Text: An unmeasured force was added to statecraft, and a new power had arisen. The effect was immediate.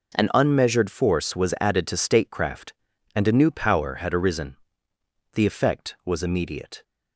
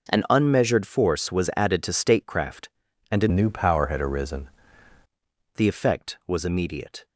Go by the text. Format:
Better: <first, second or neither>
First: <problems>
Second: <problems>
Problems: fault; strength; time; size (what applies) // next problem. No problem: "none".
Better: first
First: none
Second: changes voice from "new" to "arisen"; from 3.3 to 4.4 s; 1.1 s long